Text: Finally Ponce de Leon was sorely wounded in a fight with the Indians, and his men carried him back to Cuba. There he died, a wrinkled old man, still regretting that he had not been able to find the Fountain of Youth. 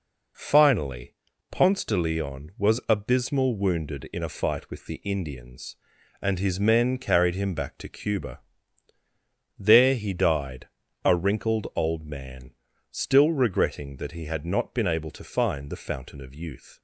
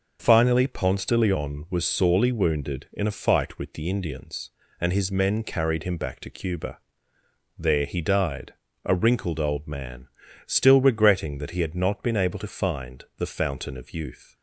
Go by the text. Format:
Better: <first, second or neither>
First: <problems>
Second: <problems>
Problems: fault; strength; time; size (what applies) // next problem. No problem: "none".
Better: second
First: pauses between "Finally" and "Ponce"; slight; at 1.1 s; 0.36 s long // says "abysmal" for "sorely"; at 2.8 s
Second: none